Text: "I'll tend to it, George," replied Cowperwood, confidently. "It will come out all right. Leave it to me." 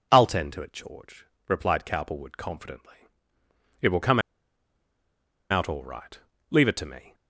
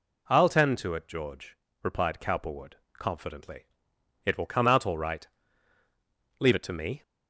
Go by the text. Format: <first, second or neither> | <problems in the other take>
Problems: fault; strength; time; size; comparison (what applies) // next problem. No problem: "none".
second | pauses between "come" and "out"; strong; at 4.1 s; 1.3 s long